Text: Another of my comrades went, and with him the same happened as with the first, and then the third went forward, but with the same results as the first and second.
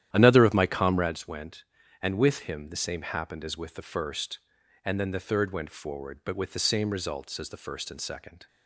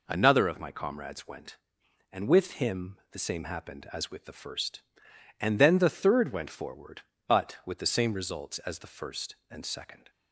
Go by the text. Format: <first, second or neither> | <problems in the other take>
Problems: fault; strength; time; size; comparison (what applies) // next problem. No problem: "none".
second | starts louder than the rest; strong; until 1.2 s; 11 dB